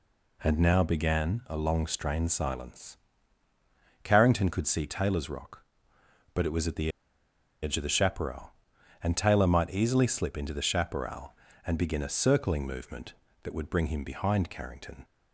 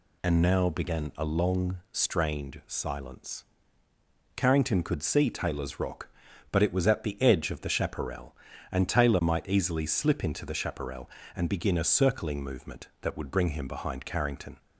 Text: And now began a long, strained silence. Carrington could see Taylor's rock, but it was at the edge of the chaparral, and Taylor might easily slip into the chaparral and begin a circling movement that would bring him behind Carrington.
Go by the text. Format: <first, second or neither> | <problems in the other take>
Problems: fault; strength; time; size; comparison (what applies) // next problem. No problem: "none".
second | pauses between "the" and "edge"; noticeable; at 6.8 s; 0.72 s long